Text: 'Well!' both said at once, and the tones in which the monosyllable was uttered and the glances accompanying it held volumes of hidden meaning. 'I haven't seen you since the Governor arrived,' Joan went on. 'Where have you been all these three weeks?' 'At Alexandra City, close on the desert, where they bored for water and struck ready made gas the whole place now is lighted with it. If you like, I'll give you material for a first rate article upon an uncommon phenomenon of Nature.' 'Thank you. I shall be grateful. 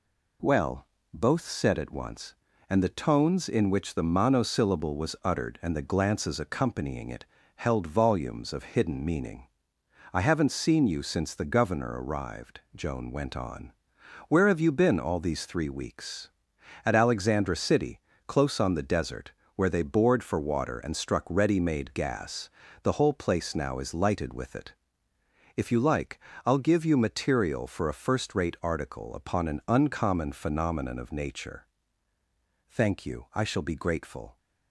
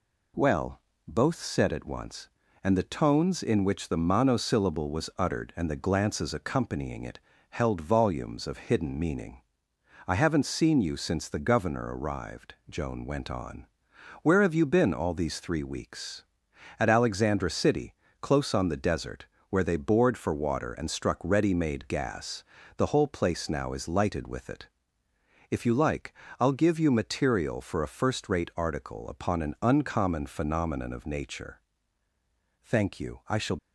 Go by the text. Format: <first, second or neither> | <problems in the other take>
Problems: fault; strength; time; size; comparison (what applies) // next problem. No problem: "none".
first | pauses between "it" and "held"; slight; at 7.1 s; 0.32 s long; slight in the first // pauses between "gas" and "the"; slight; at 22.4 s; 0.32 s long; slight in the first // stops before "be grateful"; at 33.5 s